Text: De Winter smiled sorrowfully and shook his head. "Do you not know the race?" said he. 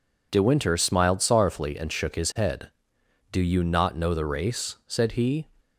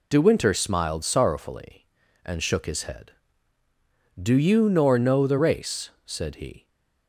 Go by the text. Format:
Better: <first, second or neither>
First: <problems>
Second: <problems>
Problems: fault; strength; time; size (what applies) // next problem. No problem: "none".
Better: first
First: none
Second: says "nor" for "not"; at 4.6 s // stays silent after the last word; slight; from 6.5 s on; 0.5 s long